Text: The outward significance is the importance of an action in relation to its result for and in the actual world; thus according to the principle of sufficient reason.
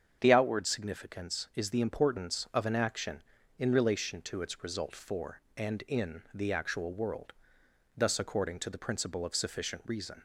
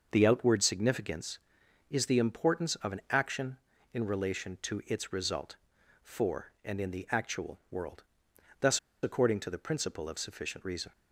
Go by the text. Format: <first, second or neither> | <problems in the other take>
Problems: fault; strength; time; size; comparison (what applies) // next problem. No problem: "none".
first | starts louder than the rest; noticeable; until 1.1 s; 6 dB; strong in the first // pauses between "thus" and "according"; slight; at 8.7 s; 0.24 s long